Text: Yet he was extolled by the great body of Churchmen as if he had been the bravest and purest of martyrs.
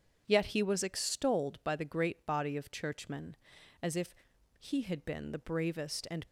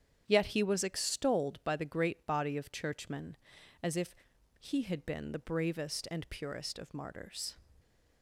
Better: second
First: starts louder than the rest; strong; until 1.2 s; 8 dB // pauses between "if" and "he"; at 4.1 s; 0.44 s long // stops before "purest of martyrs"; at 6.2 s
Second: starts louder than the rest; strong; until 1.2 s; 8.5 dB // pauses between "if" and "he"; at 4.1 s; 0.44 s long

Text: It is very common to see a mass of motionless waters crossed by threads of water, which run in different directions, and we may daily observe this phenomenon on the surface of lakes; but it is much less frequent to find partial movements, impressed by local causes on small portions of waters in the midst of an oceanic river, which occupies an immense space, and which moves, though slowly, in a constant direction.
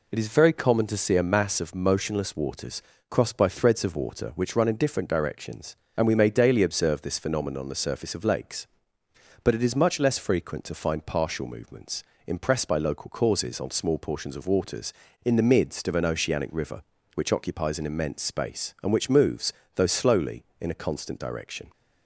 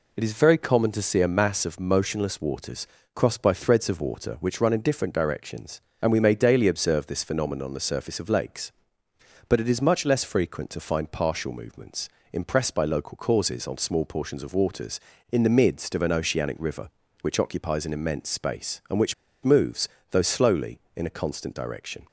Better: first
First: pauses between "waters" and "crossed"; slight; at 2.8 s; 0.28 s long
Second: pauses between "waters" and "crossed"; slight; at 2.8 s; 0.28 s long // pauses between "which" and "moves"; slight; at 19.1 s; 0.31 s long

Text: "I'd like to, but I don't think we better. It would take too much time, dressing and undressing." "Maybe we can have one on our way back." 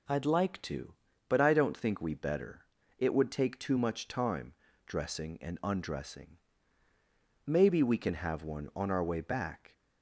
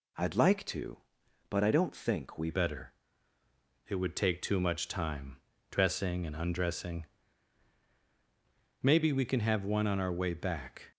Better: first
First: none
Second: changes voice at "better"; from 2.4 s on; 8.5 s long

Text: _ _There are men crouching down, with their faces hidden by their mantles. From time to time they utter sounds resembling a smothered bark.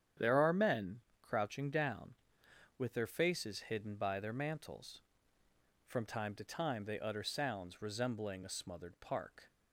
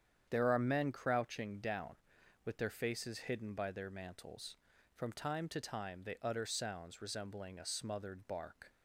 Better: second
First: starts louder than the rest; strong; until 1.4 s; 9 dB // pauses between "men" and "crouching"; slight; at 0.9 s; 0.22 s long // says "park" for "bark"; at 8.9 s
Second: starts louder than the rest; strong; until 1.3 s; 8.5 dB

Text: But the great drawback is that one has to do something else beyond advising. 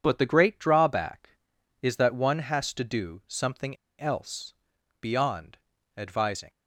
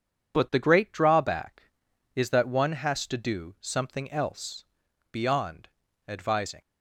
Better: second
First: pauses between "something" and "else"; slight; at 3.7 s; 0.23 s long // pauses between "else" and "beyond"; noticeable; at 4.5 s; 0.48 s long // pauses between "beyond" and "advising"; at 5.5 s; 0.40 s long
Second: pauses between "else" and "beyond"; noticeable; at 4.6 s; 0.48 s long // pauses between "beyond" and "advising"; at 5.6 s; 0.40 s long

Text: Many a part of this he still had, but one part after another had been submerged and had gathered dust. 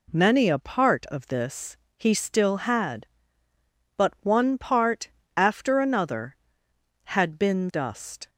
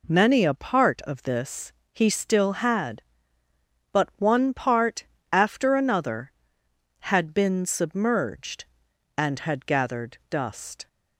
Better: second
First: pauses between "this" and "he"; slight; at 1.7 s; 0.22 s long // pauses between "part" and "after"; slight; at 5.0 s; 0.28 s long // skips "submerged and had gathered"; at 7.7 s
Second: pauses between "this" and "he"; slight; at 1.7 s; 0.22 s long // pauses between "part" and "after"; slight; at 5.0 s; 0.28 s long

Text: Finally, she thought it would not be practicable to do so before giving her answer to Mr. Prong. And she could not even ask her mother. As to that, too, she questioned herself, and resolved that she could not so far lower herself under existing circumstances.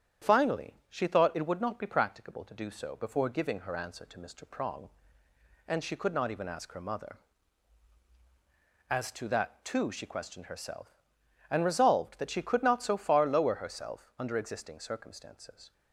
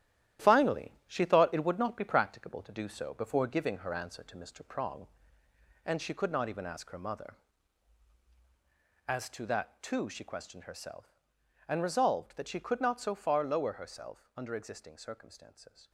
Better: first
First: starts louder than the rest; strong; until 1.3 s; 9.5 dB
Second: gets quieter; strong; throughout; 9 dB // starts louder than the rest; strong; until 1.5 s; 12.5 dB

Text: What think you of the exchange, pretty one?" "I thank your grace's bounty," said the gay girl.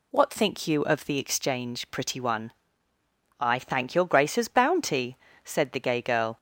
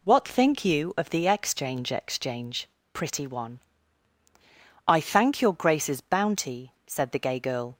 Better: first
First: none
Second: says "exchange" twice; at 1.9 s

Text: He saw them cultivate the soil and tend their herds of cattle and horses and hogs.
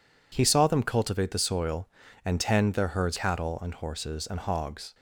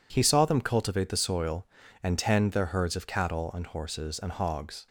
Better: second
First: skips "of"; at 3.1 s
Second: none

